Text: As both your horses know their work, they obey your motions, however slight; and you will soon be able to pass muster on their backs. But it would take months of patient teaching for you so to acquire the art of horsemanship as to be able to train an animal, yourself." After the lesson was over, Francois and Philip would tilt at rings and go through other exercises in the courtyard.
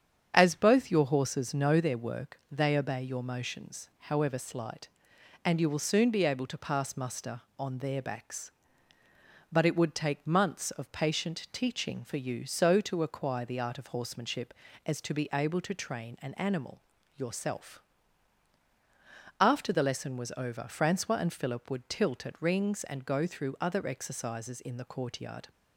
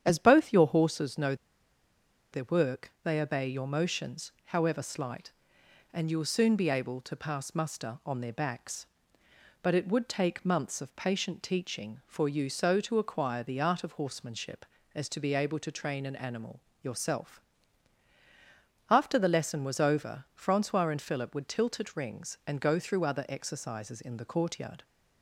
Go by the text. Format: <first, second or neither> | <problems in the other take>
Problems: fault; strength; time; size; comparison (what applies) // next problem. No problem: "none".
first | starts louder than the rest; strong; until 1.0 s; 9 dB; strong in the first // pauses between "know" and "their"; noticeable; at 1.3 s; 0.97 s long